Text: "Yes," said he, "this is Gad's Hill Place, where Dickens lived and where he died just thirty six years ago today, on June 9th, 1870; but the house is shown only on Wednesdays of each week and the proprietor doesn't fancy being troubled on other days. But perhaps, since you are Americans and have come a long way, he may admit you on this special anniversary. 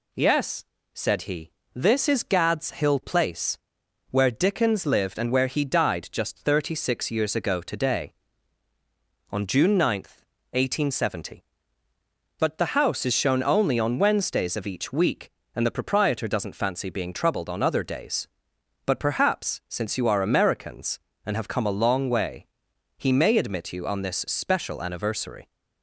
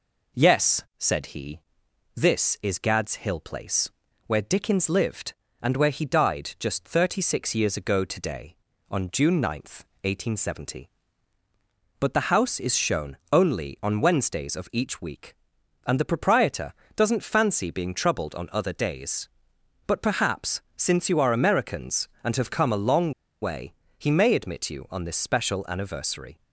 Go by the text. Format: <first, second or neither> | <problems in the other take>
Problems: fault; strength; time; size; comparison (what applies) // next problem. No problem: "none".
first | pauses between "shown" and "only"; slight; at 13.1 s; 0.16 s long // pauses between "proprietor" and "doesn't"; slight; at 16.7 s; 0.24 s long // pauses between "long" and "way"; slight; at 23.1 s; 0.30 s long